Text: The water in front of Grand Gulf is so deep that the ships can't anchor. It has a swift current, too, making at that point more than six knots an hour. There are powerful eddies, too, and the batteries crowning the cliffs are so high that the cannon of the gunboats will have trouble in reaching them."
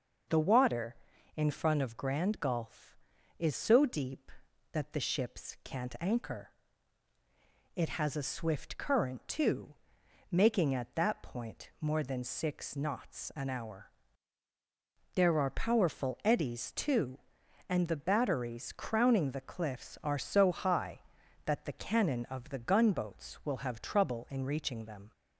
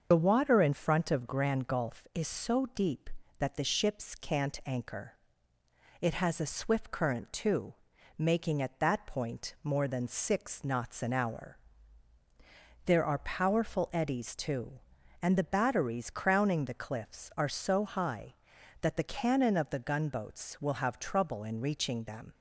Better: first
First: starts louder than the rest; noticeable; until 1.7 s; 6 dB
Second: loses the start of "The"; at 0.1 s; 50 ms // starts louder than the rest; until 1.1 s; 6.5 dB

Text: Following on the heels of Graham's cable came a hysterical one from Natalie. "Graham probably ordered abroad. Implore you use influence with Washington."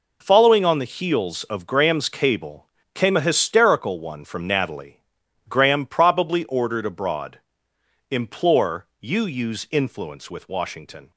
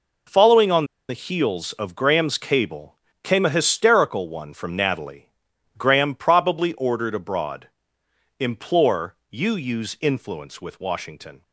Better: first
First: pauses between "cable" and "came"; slight; at 2.6 s; 0.26 s long // pauses between "Implore" and "you"; slight; at 8.8 s; 0.15 s long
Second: pauses between "on" and "the"; slight; at 0.8 s; 0.25 s long // pauses between "cable" and "came"; slight; at 2.9 s; 0.26 s long // pauses between "Implore" and "you"; slight; at 9.1 s; 0.16 s long

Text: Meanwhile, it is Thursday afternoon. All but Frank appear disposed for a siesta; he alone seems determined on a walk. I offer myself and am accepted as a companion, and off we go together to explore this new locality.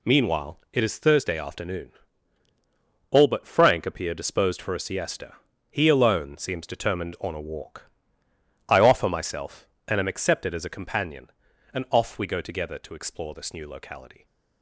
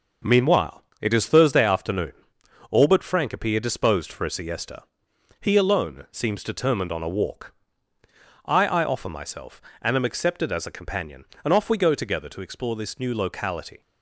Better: first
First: none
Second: says "I" twice; at 8.6 s

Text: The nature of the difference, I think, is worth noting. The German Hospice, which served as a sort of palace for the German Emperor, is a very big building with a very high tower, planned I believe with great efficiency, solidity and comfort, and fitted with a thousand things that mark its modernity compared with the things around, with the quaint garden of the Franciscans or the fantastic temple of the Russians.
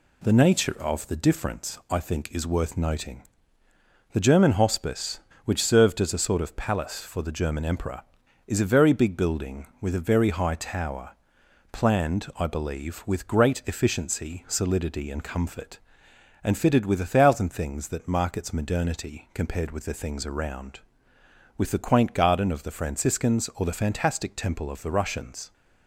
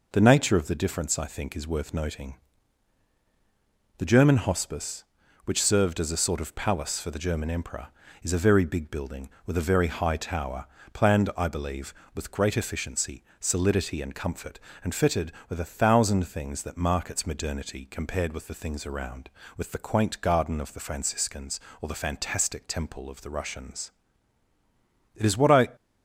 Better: first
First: none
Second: goes on to say "It is what I"; from 25.1 s on; 0.54 s long

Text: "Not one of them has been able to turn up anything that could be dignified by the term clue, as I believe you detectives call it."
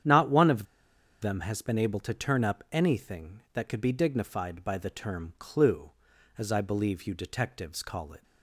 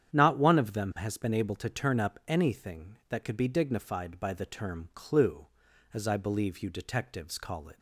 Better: second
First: starts louder than the rest; strong; until 1.6 s; 9 dB // pauses between "of" and "them"; noticeable; at 0.6 s; 0.59 s long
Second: starts louder than the rest; strong; until 1.1 s; 9 dB

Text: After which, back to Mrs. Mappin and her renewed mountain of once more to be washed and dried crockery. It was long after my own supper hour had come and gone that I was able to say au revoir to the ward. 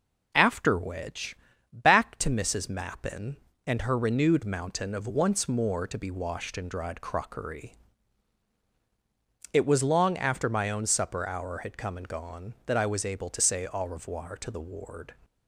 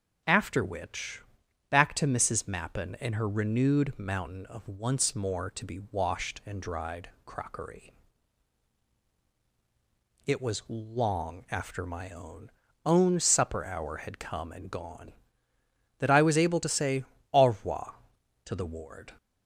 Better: first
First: none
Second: pauses between "dried" and "crockery"; slight; at 7.0 s; 0.16 s long // says "own" twice; at 12.8 s // pauses between "say" and "au"; slight; at 17.0 s; 0.28 s long

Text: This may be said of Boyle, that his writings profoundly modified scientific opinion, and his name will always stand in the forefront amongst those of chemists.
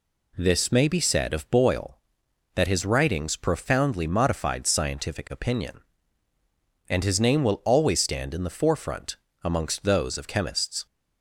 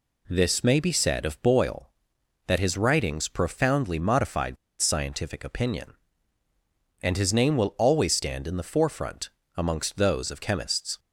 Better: first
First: pauses between "forefront" and "amongst"; slight; at 9.1 s; 0.28 s long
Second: pauses between "modified" and "scientific"; slight; at 4.5 s; 0.24 s long // pauses between "forefront" and "amongst"; slight; at 9.2 s; 0.28 s long

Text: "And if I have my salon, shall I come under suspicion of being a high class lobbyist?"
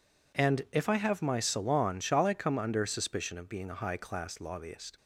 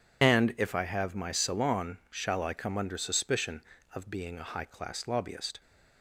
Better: first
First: none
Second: loses the start of "And"; at 0.2 s; 45 ms

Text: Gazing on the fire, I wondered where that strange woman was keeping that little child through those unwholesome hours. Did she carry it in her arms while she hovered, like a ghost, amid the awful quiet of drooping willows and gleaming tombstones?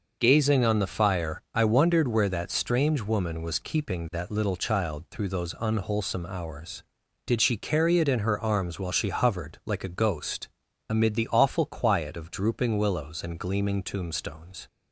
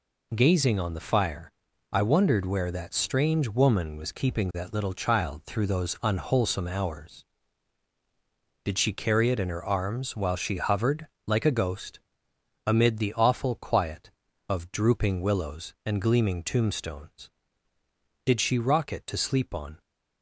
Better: first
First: none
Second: goes on to say "Did she rock it to sleep on"; from 18.2 s on; 1.5 s long

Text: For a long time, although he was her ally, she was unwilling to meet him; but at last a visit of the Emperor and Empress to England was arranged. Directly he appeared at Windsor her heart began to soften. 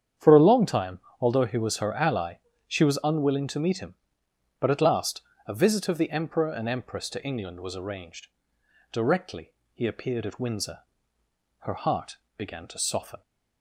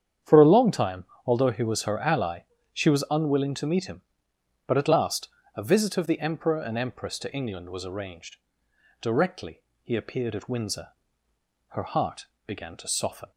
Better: neither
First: starts louder than the rest; strong; until 1.4 s; 8.5 dB // pauses between "last" and "a"; slight; at 5.2 s; 0.26 s long // pauses between "Directly" and "he"; slight; at 9.5 s; 0.22 s long // pauses between "Windsor" and "her"; noticeable; at 10.7 s; 0.82 s long // pauses between "heart" and "began"; slight; at 12.1 s; 0.18 s long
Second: starts louder than the rest; strong; until 1.4 s; 8.5 dB // pauses between "last" and "a"; slight; at 5.2 s; 0.28 s long // pauses between "Directly" and "he"; slight; at 9.6 s; 0.22 s long // pauses between "Windsor" and "her"; noticeable; at 10.8 s; 0.82 s long // pauses between "heart" and "began"; slight; at 12.2 s; 0.18 s long

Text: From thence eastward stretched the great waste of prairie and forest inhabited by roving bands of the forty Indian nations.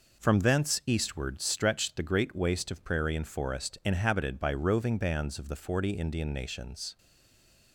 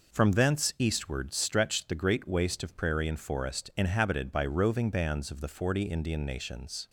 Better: second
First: stays silent after the last word; slight; from 6.9 s on; 0.8 s long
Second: none

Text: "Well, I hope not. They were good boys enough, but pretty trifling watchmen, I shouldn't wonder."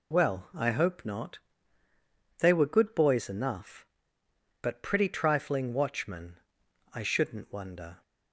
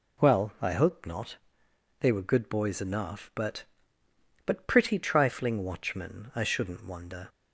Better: first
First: none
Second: says "but" twice; at 4.4 s

